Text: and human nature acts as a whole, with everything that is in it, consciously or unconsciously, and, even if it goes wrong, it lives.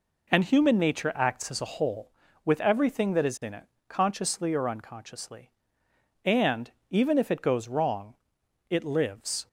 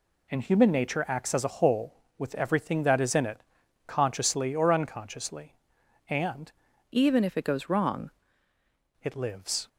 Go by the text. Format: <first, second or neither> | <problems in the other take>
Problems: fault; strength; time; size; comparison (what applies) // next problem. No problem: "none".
first | changes voice from "even" to "wrong"; from 6.9 to 8.1 s; 1.2 s long